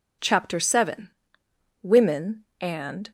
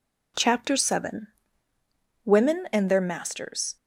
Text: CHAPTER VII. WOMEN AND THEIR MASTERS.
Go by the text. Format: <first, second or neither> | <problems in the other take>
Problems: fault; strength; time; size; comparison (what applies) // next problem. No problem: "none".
second | stops before "THEIR MASTERS"; at 3.0 s